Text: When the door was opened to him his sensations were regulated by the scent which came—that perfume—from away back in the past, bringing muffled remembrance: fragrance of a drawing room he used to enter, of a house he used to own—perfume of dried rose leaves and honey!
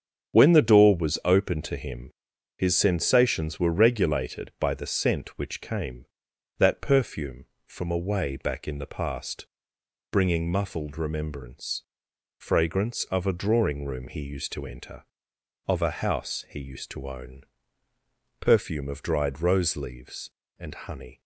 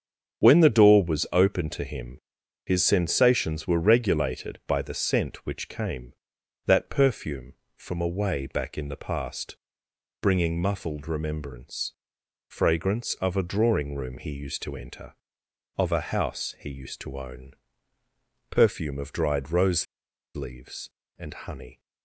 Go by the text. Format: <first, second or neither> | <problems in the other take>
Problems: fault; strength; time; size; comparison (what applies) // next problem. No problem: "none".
first | starts louder than the rest; strong; until 1.4 s; 7 dB; strong in the first // pauses between "him" and "his"; noticeable; at 2.2 s; 0.46 s long; noticeable in the first // pauses between "rose" and "leaves"; noticeable; at 19.8 s; 0.50 s long